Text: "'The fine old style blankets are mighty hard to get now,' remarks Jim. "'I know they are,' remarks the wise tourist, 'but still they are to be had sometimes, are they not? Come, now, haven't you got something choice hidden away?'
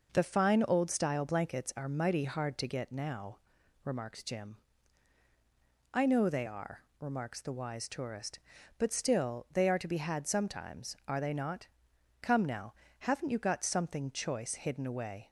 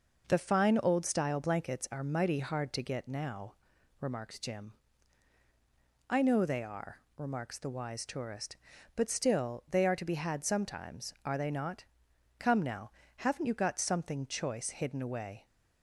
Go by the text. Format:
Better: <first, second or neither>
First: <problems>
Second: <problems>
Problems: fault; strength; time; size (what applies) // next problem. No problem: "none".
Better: neither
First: none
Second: none